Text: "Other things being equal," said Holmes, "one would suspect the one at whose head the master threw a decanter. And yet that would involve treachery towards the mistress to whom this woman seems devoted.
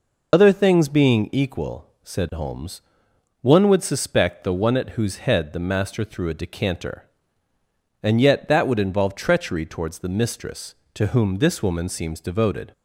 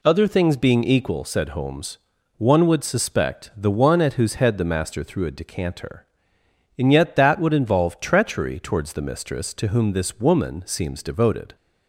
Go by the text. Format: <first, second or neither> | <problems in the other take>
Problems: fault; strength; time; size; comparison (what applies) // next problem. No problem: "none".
second | loses the start of "Other"; at 0.3 s; 70 ms